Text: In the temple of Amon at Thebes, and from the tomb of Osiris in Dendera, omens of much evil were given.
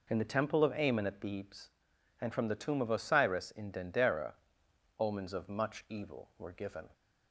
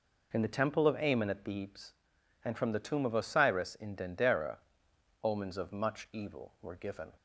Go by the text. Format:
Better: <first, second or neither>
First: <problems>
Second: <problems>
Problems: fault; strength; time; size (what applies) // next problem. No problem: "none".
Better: neither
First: none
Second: none